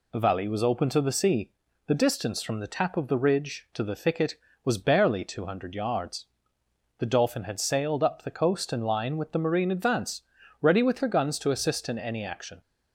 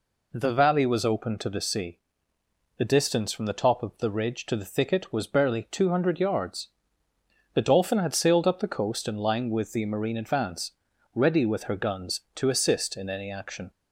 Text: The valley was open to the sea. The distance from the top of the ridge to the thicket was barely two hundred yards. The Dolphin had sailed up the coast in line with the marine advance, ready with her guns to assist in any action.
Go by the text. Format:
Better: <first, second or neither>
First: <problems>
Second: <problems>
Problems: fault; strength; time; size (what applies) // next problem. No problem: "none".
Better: second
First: says "tap" for "top"; at 2.6 s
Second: none